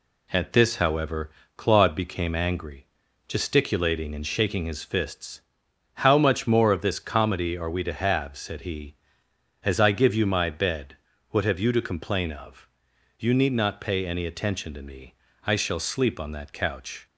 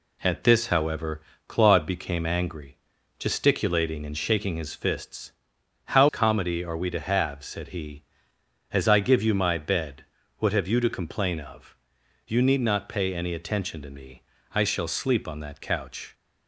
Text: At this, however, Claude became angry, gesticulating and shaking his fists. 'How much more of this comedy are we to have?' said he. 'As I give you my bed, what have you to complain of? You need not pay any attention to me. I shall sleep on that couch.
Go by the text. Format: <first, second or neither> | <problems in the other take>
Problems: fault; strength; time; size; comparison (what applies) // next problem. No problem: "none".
first | skips "much more of this"; at 6.0 s